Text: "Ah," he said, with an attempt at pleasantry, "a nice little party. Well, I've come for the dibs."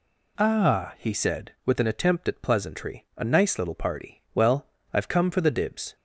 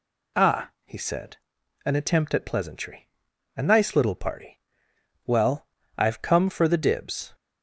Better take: first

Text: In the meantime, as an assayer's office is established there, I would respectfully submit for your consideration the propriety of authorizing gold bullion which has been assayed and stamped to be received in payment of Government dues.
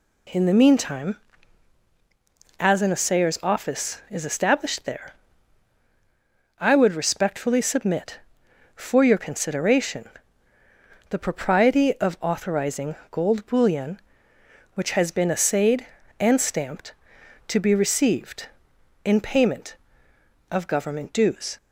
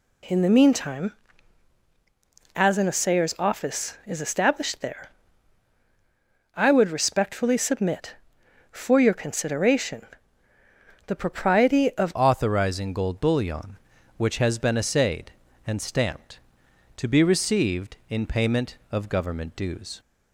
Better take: first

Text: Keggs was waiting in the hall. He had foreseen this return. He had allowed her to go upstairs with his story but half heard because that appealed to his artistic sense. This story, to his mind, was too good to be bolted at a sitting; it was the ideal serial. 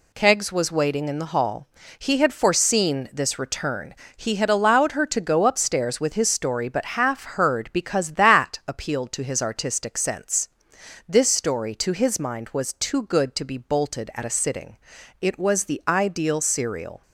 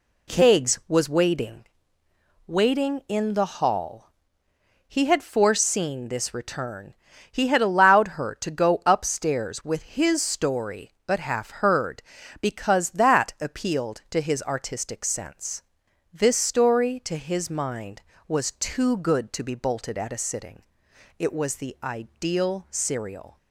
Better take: first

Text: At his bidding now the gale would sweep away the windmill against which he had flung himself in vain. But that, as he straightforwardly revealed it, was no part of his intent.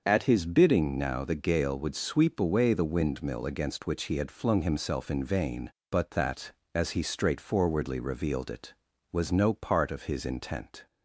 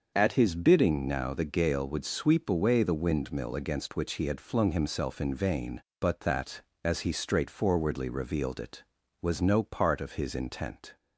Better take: neither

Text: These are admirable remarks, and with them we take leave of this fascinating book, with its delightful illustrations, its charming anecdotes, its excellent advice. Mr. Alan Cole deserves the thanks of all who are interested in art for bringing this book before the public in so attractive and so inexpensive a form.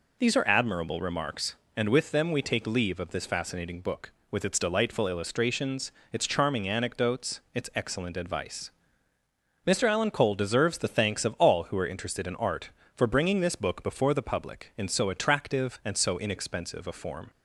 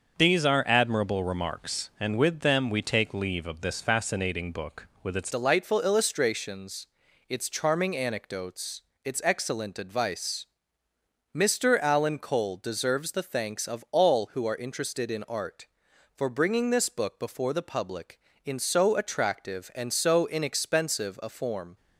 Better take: first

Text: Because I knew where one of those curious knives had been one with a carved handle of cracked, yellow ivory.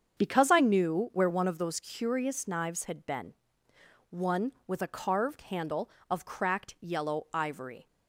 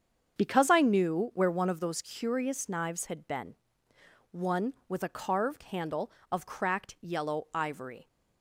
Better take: neither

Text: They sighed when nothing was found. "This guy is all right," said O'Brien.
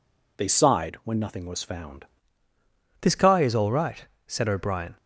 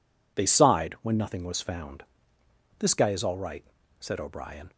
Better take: second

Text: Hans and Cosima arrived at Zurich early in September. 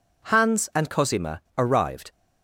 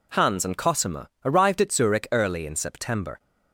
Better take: second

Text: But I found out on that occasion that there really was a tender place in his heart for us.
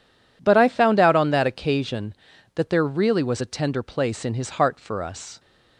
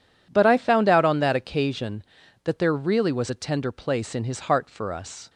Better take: neither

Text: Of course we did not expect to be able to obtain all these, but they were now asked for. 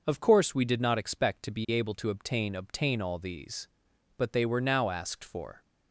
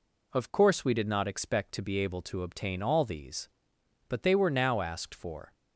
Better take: second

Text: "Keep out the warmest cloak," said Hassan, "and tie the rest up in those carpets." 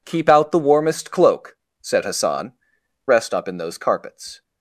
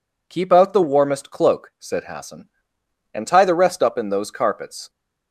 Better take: second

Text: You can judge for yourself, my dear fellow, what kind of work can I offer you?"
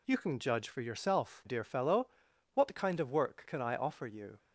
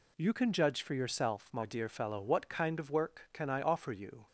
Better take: second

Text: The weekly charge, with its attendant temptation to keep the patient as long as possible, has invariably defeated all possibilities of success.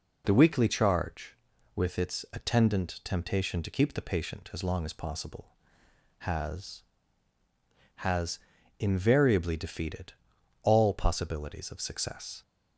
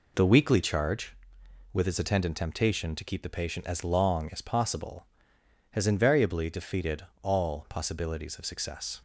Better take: second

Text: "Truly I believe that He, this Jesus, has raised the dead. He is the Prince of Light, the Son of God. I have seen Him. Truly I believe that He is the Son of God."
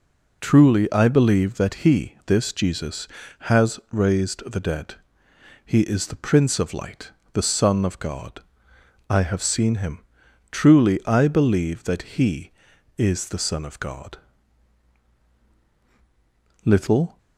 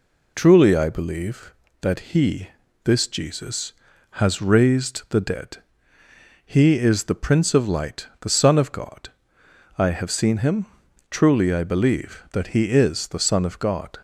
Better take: second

